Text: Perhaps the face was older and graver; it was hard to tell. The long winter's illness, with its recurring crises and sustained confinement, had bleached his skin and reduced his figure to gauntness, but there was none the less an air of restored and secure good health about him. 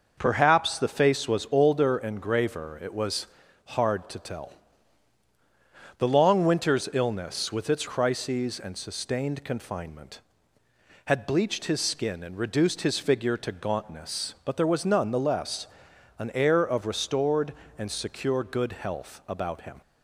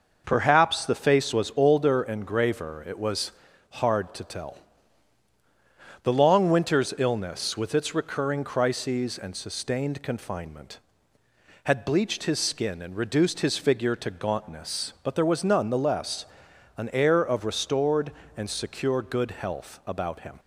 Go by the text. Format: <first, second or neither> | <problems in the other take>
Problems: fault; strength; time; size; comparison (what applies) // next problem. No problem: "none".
second | pauses between "was" and "hard"; at 3.2 s; 0.40 s long; also in the second // skips "recurring"; at 7.8 s // pauses between "less" and "an"; noticeable; at 15.6 s; 0.52 s long; noticeable in the second